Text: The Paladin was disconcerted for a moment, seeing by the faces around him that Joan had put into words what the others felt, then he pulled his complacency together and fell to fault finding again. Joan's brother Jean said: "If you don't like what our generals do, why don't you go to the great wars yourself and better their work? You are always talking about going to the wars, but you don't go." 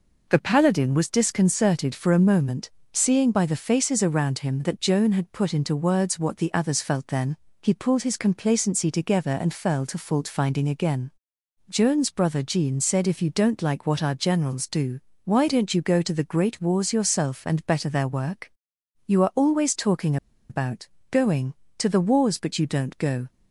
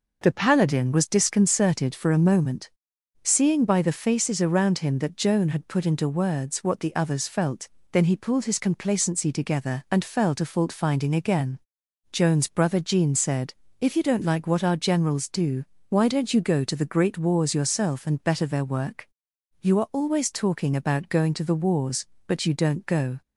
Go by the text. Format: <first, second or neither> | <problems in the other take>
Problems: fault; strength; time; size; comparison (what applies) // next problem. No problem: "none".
second | pauses between "then" and "he"; slight; at 7.3 s; 0.26 s long // pauses between "talking" and "about"; slight; at 20.1 s; 0.33 s long // pauses between "about" and "going"; slight; at 20.8 s; 0.22 s long